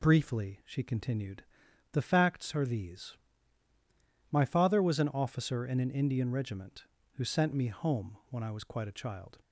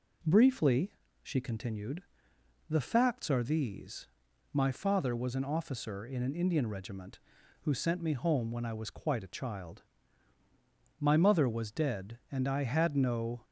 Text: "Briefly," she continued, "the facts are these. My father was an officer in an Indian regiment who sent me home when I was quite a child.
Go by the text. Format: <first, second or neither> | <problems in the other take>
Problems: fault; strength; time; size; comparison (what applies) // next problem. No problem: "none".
first | goes on to say "My mother was dead and I had no"; strong; from 11.0 s on; 2.4 s long